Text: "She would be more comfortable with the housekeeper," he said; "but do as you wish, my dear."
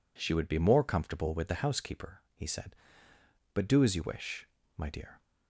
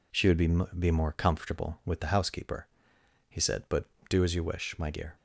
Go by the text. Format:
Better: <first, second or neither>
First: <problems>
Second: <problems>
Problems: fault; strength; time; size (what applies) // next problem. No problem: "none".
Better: first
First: none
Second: says "be" twice; at 0.7 s